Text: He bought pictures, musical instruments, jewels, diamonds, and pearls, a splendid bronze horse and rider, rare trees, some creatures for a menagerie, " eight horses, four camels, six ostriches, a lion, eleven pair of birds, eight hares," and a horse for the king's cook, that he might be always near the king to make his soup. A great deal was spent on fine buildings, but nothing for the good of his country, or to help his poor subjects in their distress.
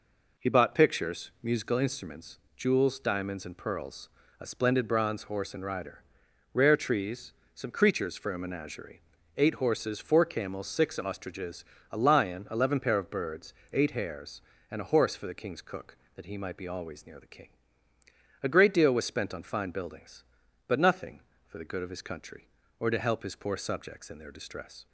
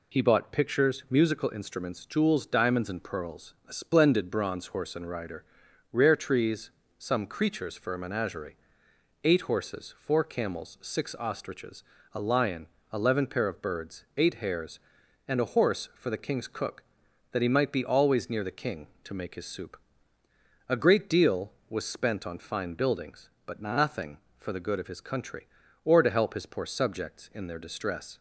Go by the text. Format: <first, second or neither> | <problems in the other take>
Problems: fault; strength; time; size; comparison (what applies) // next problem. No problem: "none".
second | skips "to make his soup"; at 17.9 s